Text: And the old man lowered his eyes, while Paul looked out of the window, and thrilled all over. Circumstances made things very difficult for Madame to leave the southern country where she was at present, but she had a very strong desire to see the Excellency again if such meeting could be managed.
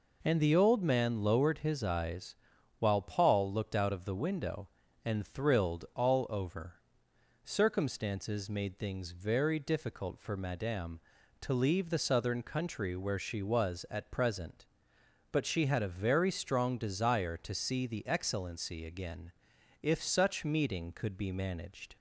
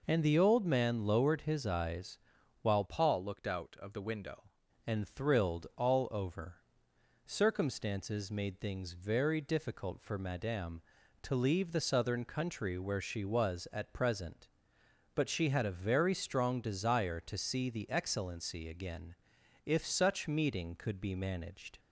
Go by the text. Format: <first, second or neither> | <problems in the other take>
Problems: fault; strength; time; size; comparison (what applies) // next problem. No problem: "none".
first | changes voice from "Paul" to "window"; from 2.8 to 4.5 s; 1.7 s long // pauses between "again" and "if"; noticeable; at 19.1 s; 0.50 s long; noticeable in the first